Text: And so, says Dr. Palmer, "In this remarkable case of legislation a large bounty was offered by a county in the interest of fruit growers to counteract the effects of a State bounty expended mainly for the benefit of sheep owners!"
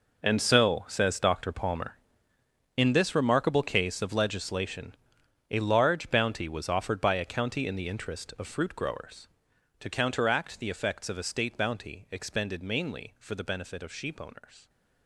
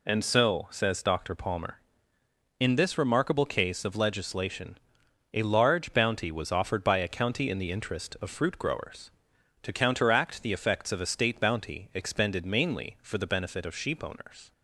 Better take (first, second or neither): second